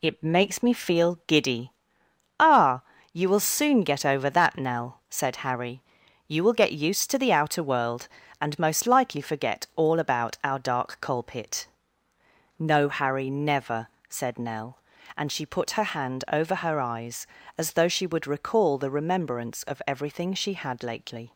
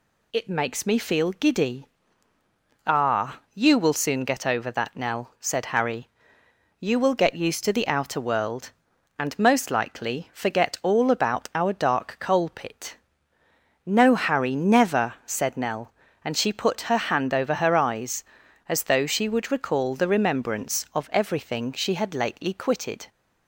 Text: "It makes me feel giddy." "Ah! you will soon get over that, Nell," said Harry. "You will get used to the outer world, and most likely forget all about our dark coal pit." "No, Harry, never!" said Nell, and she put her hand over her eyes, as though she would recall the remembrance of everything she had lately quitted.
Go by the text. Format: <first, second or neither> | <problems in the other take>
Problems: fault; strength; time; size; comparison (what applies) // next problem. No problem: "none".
second | stops before "quitted"; at 21.3 s